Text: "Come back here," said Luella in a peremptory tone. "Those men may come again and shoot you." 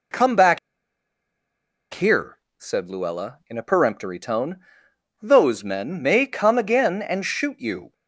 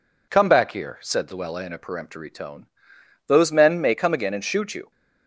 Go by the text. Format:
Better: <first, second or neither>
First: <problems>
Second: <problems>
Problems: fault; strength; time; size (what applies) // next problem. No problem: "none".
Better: second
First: pauses between "back" and "here"; strong; at 0.5 s; 1.3 s long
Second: none